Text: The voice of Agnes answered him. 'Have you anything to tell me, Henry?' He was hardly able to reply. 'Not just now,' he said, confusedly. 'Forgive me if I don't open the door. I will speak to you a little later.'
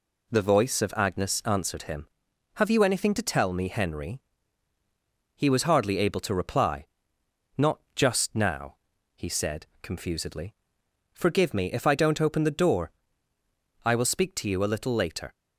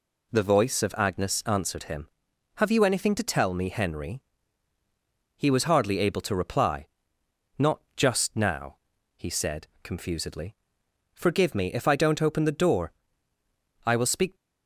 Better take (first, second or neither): first